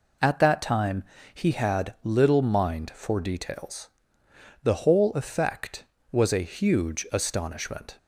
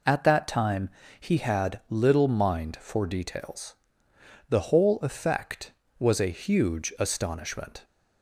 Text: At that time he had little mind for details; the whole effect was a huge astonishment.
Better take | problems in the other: neither | pauses between "time" and "he"; slight; the same in both

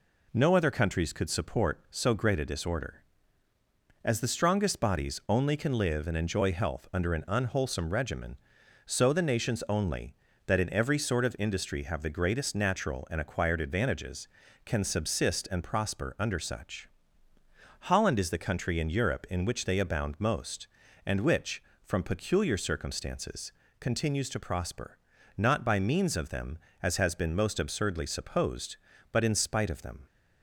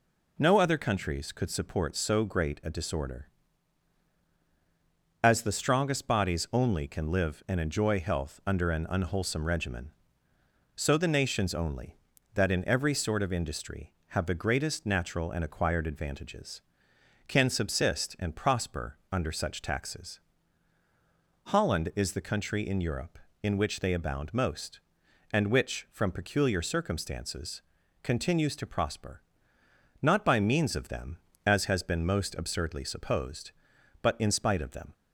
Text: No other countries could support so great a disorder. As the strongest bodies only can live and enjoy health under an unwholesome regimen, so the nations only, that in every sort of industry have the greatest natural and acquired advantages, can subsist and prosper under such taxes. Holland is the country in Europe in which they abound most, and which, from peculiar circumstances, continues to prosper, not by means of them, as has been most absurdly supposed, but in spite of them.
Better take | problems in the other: second | skips "taxes"; at 17.3 s

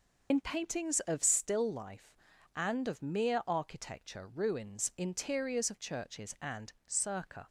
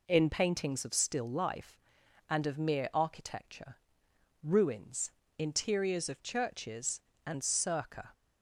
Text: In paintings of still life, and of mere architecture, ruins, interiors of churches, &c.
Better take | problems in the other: second | loses the start of "In"; at 0.3 s; 70 ms

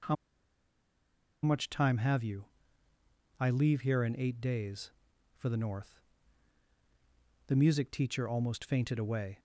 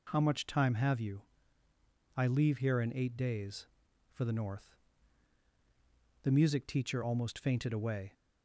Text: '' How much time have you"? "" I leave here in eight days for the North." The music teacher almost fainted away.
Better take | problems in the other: second | pauses between "How" and "much"; strong; at 0.1 s; 1.2 s long

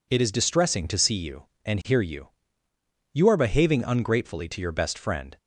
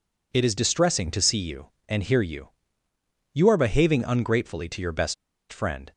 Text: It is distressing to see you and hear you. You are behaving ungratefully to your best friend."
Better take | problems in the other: first | pauses between "best" and "friend"; at 5.1 s; 0.37 s long

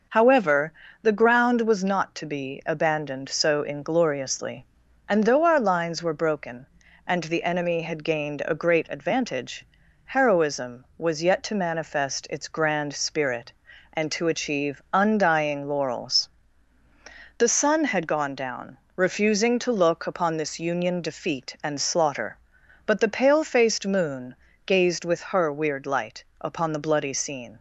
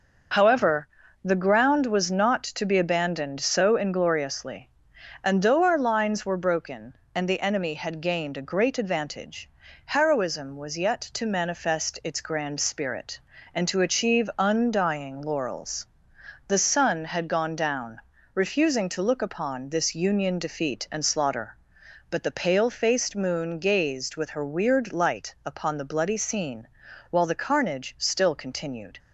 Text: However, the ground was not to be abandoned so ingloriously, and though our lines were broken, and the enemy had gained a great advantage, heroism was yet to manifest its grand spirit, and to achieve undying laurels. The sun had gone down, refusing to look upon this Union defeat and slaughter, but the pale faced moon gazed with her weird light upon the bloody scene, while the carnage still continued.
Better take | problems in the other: second | pauses between "moon" and "gazed"; slight; at 24.3 s; 0.28 s long // pauses between "light" and "upon"; slight; at 26.2 s; 0.16 s long // stops before "while the carnage still continued"; at 27.5 s

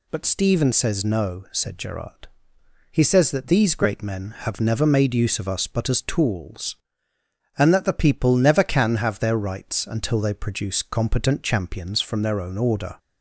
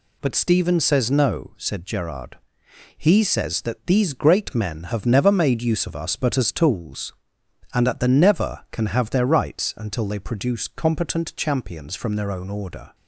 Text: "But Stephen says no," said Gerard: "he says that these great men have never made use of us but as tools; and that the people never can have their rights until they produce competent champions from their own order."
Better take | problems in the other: first | skips "people"; at 8.0 s

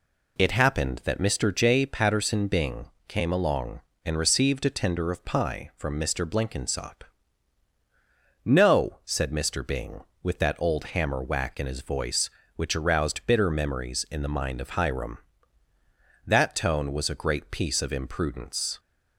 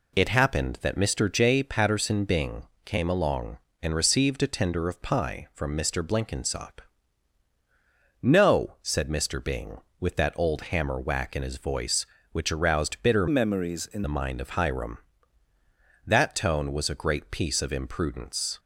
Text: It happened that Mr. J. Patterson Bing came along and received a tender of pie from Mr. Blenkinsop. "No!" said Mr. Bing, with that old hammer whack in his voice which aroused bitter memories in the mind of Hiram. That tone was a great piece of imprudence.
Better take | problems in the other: first | pauses between "Bing" and "came"; slight; at 2.6 s; 0.22 s long; slight in the first // changes voice from "memories" to "in"; from 13.2 to 14.0 s; 0.8 s long

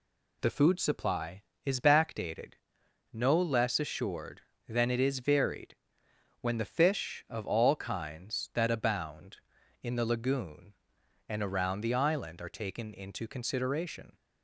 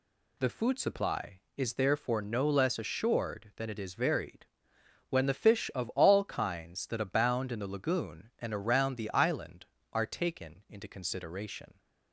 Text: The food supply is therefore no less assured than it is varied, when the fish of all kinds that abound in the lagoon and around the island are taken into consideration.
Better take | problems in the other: second | says "backdated" for "therefore"; at 1.8 s

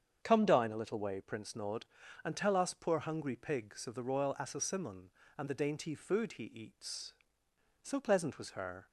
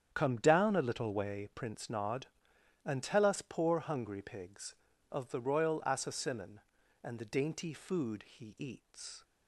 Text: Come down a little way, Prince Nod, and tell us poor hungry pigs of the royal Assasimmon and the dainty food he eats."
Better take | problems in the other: second | starts louder than the rest; strong; until 1.2 s; 7.5 dB; strong in the second // goes on to say "So pleasant was her"; noticeable; from 7.8 s on; 1.0 s long

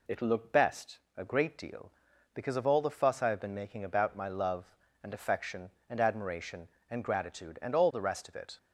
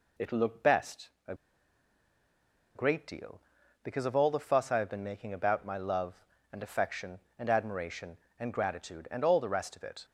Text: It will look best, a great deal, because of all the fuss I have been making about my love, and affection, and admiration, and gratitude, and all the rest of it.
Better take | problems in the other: first | pauses between "a" and "great"; strong; at 1.3 s; 1.4 s long

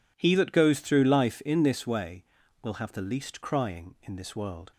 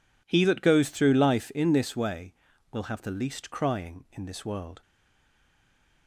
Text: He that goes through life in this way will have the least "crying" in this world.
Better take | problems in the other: first | stays silent after the last word; noticeable; from 4.8 s on; 1.2 s long

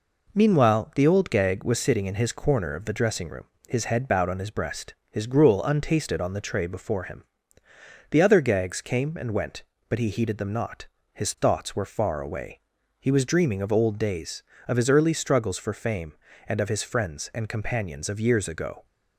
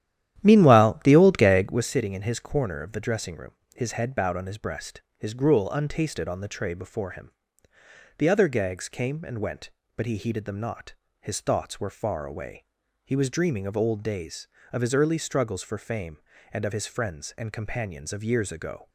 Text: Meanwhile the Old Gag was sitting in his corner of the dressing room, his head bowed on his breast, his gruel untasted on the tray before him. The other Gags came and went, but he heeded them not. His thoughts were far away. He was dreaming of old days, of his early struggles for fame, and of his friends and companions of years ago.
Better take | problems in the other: first | starts louder than the rest; strong; until 1.8 s; 11.5 dB

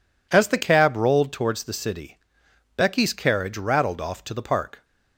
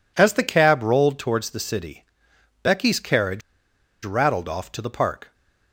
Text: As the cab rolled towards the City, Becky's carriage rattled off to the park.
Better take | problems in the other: first | pauses between "carriage" and "rattled"; noticeable; at 3.4 s; 0.64 s long

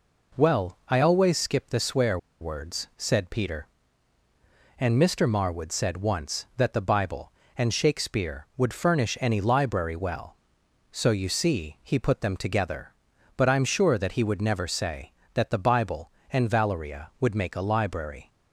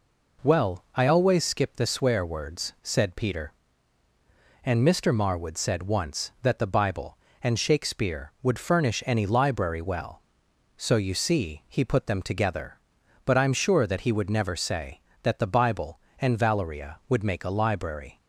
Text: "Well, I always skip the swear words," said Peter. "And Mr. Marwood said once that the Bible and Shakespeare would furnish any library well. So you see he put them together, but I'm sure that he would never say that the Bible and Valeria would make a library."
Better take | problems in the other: second | pauses between "swear" and "words"; slight; at 2.1 s; 0.23 s long

